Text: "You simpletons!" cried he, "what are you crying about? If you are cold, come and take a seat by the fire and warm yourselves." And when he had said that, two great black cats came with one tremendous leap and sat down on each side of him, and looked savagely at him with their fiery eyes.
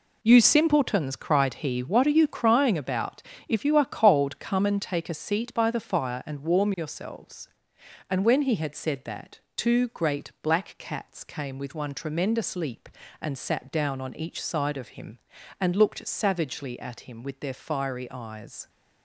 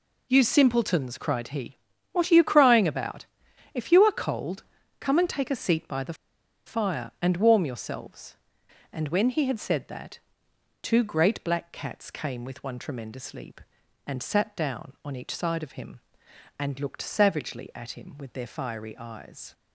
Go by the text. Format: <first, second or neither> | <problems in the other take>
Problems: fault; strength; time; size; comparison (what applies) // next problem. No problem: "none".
first | pauses between "the" and "fire"; noticeable; at 6.1 s; 0.52 s long